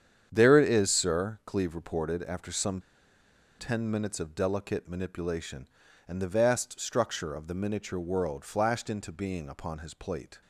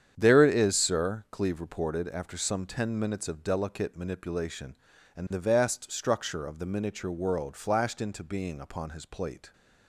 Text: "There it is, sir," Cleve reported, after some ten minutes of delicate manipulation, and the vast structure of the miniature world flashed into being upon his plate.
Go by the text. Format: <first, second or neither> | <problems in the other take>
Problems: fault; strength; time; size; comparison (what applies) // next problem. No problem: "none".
second | starts louder than the rest; strong; until 1.3 s; 8.5 dB; strong in the second // pauses between "some" and "ten"; noticeable; at 2.7 s; 0.79 s long